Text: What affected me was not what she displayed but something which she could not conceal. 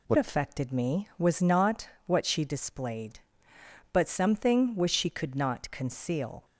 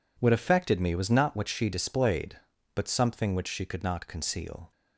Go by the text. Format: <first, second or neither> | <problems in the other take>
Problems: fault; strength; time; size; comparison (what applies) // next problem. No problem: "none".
second | changes voice at "affected"; from 0.1 s on; 6.3 s long // pauses between "not" and "what"; slight; at 1.8 s; 0.18 s long